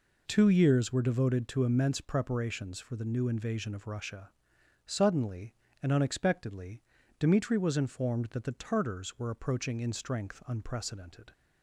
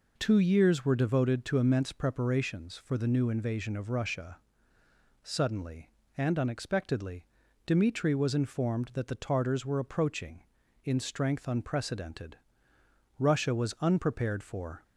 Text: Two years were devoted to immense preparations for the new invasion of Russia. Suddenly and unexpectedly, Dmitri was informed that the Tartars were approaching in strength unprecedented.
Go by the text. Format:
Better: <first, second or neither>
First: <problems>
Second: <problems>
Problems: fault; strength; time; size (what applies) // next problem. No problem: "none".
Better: first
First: none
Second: goes on to say "Russia was unprepared for"; from 13.1 s on; 1.6 s long